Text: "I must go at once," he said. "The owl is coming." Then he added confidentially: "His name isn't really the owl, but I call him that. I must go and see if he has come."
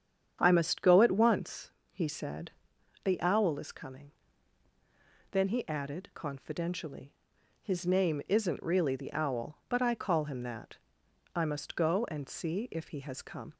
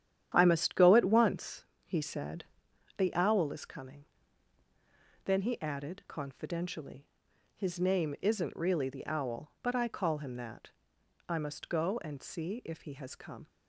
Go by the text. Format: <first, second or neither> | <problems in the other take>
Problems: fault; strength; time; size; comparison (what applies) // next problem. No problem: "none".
first | gets quieter; strong; throughout; 8 dB // starts louder than the rest; strong; until 1.3 s; 10 dB; strong in the first